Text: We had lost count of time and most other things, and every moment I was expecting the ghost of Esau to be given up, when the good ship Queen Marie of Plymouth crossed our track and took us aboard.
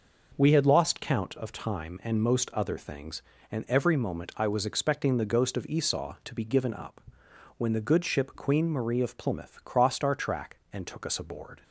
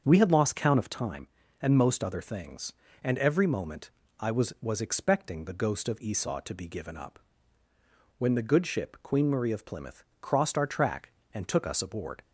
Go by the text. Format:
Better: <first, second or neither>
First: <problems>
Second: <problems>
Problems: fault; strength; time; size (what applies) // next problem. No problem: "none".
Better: first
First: none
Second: starts louder than the rest; until 1.0 s; 7 dB // pauses between "moment" and "I"; slight; at 3.8 s; 0.30 s long // says "was" twice; at 4.6 s // pauses between "Plymouth" and "crossed"; slight; at 10.0 s; 0.18 s long